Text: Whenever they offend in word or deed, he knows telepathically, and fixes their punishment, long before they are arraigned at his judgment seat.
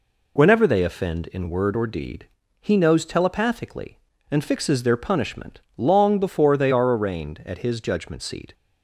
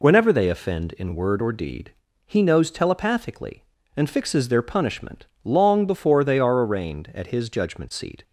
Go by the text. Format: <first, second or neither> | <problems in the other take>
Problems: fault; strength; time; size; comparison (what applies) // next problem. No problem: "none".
neither | none